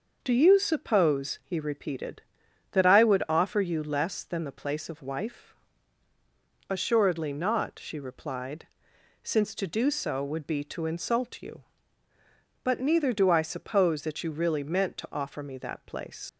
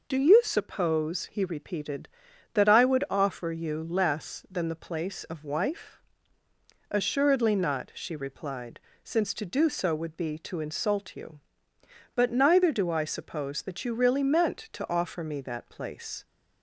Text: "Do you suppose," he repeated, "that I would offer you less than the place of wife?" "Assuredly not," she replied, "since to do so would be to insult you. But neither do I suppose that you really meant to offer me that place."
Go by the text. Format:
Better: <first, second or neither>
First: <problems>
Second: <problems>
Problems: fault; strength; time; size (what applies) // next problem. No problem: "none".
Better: second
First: leaves "place" unfinished; at 16.2 s; 90 ms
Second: none